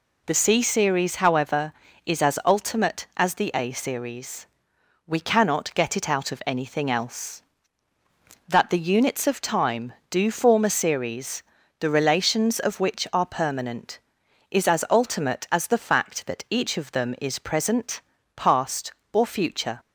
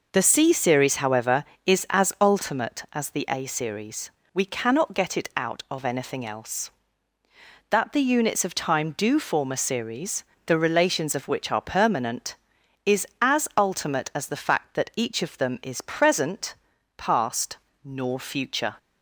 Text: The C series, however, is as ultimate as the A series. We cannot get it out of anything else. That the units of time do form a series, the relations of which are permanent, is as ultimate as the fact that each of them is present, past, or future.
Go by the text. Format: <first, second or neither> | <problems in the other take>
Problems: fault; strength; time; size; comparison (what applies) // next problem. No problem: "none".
first | says "nor" for "or"; at 17.8 s